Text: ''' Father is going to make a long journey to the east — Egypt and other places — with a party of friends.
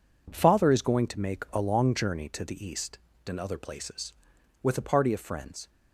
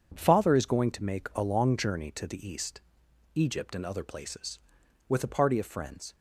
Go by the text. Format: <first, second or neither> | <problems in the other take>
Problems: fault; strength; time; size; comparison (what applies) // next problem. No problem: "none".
second | skips "Egypt"; at 3.1 s